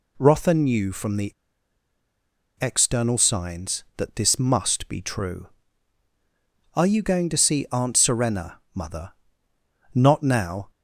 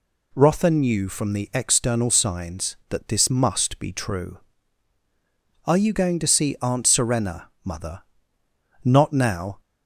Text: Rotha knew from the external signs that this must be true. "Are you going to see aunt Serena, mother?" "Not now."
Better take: second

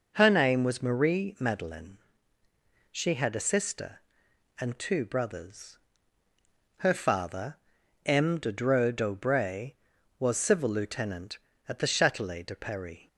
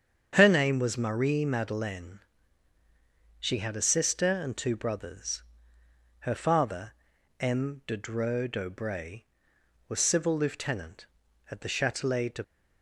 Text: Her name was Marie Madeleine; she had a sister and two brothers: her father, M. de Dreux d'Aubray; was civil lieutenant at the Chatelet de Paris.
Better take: first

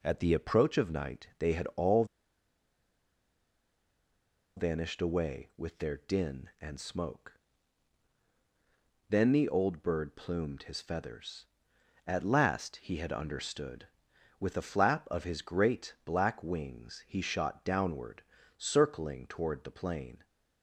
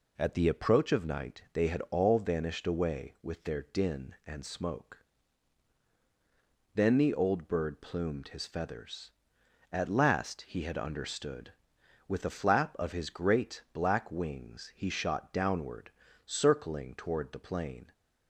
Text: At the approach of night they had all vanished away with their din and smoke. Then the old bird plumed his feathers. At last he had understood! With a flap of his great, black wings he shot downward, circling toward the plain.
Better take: second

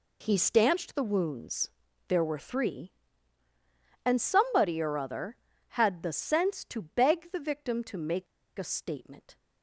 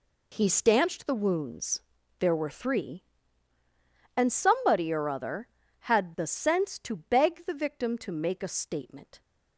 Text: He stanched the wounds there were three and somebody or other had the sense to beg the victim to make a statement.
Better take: second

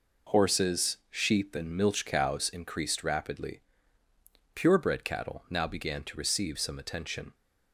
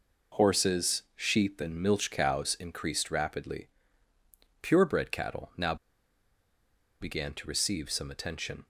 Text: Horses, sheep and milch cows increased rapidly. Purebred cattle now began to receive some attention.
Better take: first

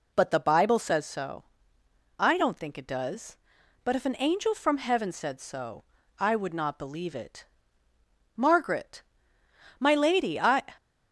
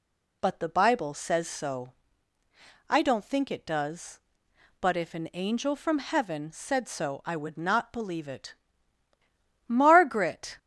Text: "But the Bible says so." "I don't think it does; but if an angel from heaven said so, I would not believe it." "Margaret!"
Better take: second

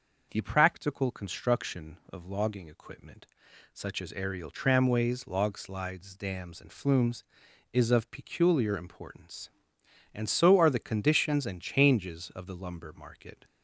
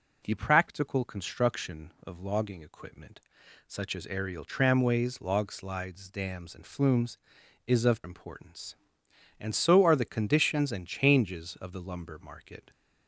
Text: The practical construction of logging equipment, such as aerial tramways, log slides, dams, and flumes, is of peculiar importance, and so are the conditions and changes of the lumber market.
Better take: first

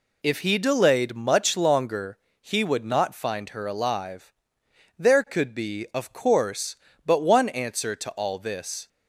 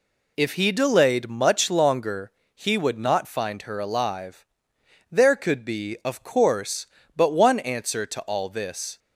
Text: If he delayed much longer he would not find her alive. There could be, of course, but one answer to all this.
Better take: neither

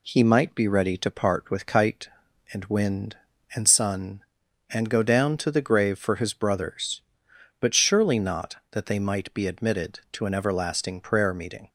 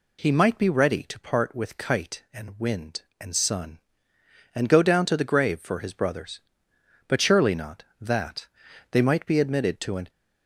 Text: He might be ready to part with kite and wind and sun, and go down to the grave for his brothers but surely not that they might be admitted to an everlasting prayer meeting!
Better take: first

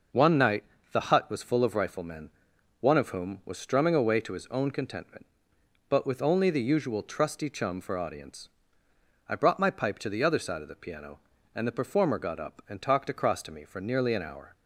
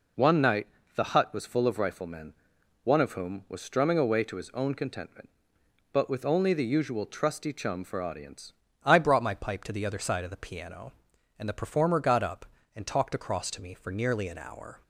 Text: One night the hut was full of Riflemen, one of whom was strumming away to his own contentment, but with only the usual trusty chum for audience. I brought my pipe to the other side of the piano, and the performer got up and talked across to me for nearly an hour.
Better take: first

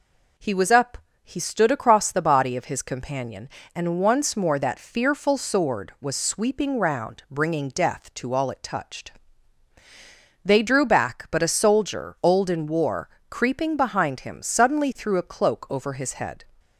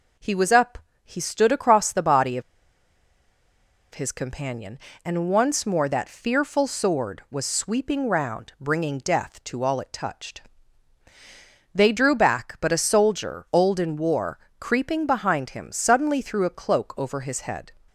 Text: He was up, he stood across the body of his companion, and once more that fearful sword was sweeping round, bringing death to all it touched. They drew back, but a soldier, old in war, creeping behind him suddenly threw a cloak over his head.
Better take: first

